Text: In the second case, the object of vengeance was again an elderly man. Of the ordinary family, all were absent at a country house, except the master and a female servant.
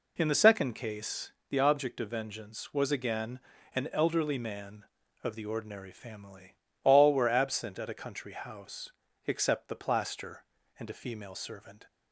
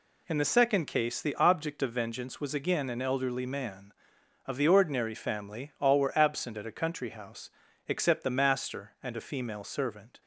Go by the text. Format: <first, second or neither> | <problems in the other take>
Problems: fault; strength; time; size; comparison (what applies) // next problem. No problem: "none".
second | pauses between "again" and "an"; slight; at 3.3 s; 0.36 s long // says "plaster" for "master"; at 9.7 s